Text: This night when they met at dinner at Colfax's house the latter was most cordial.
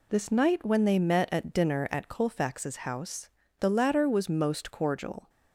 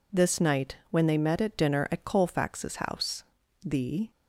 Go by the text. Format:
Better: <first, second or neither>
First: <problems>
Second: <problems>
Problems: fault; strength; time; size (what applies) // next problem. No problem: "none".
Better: first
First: pauses between "house" and "the"; slight; at 3.2 s; 0.30 s long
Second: pauses between "house" and "the"; at 3.2 s; 0.42 s long // stops before "latter was most cordial"; at 4.0 s